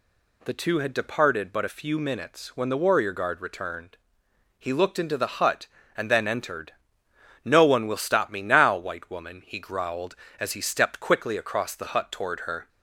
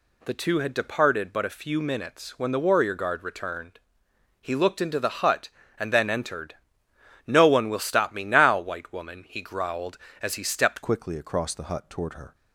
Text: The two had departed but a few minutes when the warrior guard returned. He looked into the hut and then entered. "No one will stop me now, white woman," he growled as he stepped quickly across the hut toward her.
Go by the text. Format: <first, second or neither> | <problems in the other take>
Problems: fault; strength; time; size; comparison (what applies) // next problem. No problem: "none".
first | changes voice at "quickly"; from 10.8 s on; 1.5 s long